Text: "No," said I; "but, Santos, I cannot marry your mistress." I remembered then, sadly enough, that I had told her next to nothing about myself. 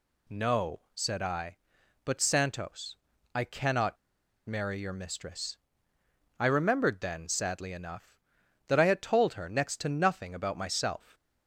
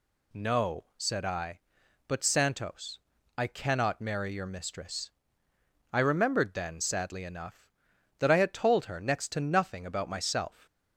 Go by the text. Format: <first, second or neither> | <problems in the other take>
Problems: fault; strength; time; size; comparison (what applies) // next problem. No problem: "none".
second | pauses between "cannot" and "marry"; noticeable; at 3.9 s; 0.49 s long